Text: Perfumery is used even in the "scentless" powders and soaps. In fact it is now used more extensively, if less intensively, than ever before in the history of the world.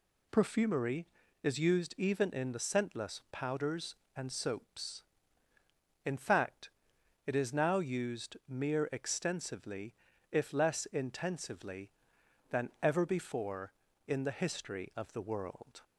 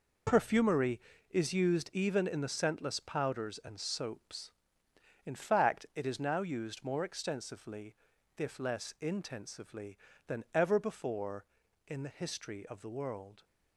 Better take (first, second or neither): second